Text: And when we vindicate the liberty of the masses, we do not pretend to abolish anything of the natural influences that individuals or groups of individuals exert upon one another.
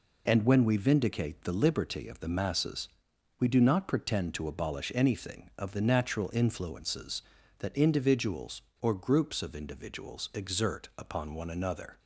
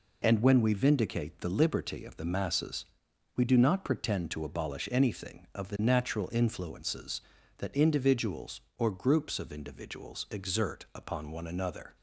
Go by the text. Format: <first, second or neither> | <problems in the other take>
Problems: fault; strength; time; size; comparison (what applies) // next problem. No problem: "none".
neither | none